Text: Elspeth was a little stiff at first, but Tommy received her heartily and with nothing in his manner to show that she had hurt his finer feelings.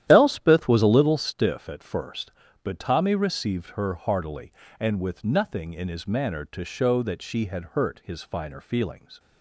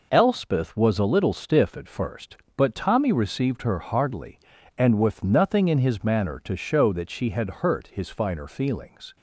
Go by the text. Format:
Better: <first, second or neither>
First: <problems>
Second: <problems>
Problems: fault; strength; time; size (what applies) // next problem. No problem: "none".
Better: second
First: starts louder than the rest; strong; until 1.0 s; 11.5 dB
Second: none